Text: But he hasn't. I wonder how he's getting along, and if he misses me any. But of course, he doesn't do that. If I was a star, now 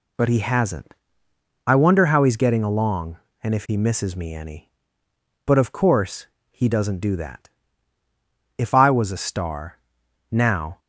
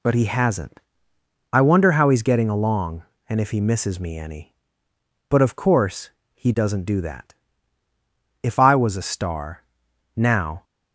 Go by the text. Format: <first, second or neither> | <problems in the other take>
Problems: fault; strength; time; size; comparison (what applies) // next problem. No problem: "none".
neither | none